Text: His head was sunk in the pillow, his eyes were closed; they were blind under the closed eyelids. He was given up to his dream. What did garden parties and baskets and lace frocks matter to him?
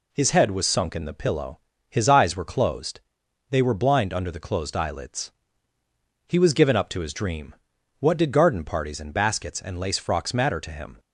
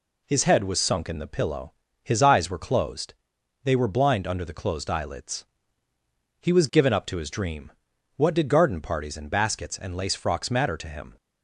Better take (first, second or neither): neither